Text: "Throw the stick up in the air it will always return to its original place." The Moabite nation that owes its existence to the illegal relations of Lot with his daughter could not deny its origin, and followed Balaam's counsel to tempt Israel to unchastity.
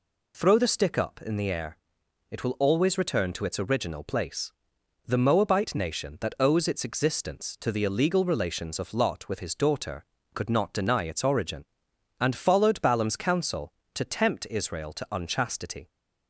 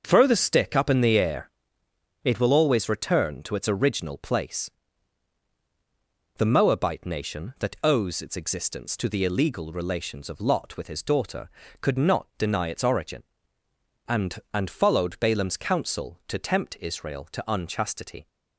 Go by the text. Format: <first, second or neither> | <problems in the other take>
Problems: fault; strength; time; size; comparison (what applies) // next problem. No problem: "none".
first | starts louder than the rest; until 1.0 s; 6 dB // pauses between "air" and "it"; noticeable; at 1.4 s; 0.74 s long; noticeable in the first // says "and" twice; at 14.5 s